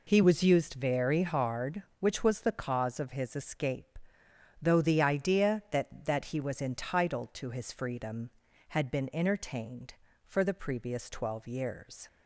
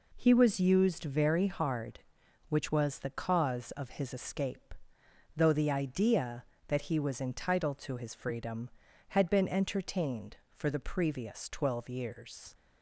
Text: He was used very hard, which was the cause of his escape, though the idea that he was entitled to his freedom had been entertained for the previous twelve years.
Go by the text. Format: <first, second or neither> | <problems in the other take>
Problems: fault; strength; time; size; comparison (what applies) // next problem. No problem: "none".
second | says "that" twice; at 6.0 s